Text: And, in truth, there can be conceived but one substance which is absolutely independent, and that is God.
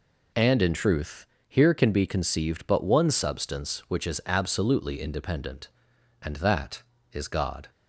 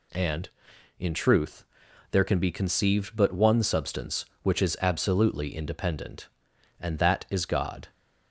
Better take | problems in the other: second | says "here" for "there"; at 1.4 s

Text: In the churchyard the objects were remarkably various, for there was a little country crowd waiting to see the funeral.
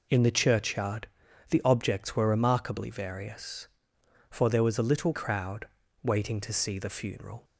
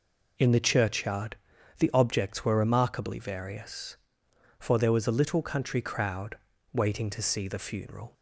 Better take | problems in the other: second | pauses between "churchyard" and "the"; at 1.0 s; 0.44 s long; also in the second // skips "country"; at 5.1 s // pauses between "crowd" and "waiting"; slight; at 5.6 s; 0.34 s long; slight in the second

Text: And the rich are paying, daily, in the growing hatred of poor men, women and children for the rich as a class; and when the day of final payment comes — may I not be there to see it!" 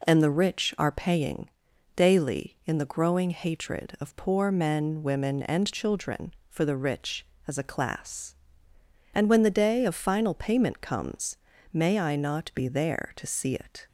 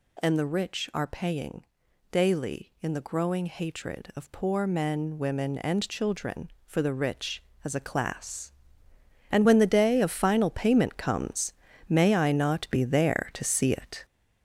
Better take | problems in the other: first | gets louder; throughout; 7 dB

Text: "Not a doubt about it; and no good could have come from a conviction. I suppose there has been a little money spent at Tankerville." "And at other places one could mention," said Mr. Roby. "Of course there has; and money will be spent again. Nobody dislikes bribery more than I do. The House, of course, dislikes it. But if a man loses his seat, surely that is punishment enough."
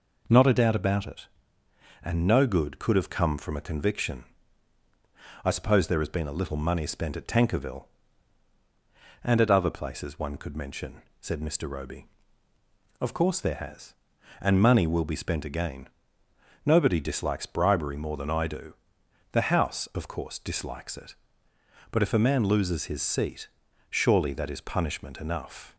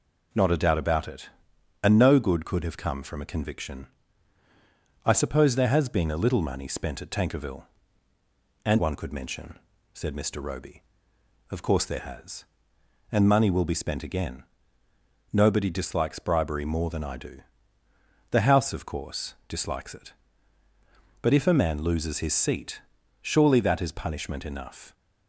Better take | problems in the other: first | skips "at other places"; at 8.7 s

